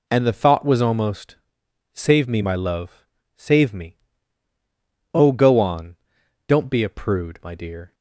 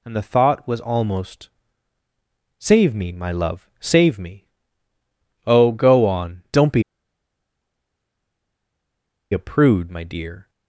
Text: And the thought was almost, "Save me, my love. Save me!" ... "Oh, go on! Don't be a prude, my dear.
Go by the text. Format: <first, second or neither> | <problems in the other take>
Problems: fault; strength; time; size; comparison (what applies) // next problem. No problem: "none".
first | pauses between "be" and "a"; strong; at 6.8 s; 2.4 s long